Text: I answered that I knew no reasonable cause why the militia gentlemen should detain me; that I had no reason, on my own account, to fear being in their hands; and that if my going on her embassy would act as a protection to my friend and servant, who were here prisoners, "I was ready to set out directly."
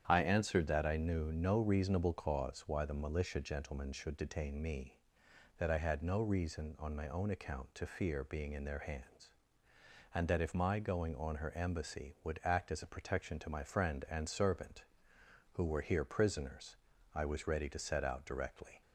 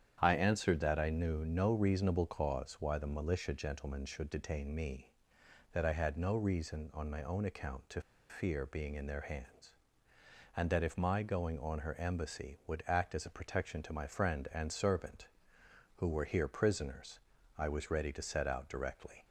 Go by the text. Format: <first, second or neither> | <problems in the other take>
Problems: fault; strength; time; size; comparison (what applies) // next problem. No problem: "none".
first | starts louder than the rest; strong; until 1.2 s; 9 dB; strong in the first // pauses between "to" and "fear"; slight; at 8.0 s; 0.28 s long